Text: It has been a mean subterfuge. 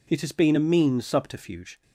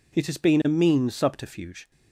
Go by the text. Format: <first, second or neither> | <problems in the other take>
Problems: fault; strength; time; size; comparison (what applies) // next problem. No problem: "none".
neither | none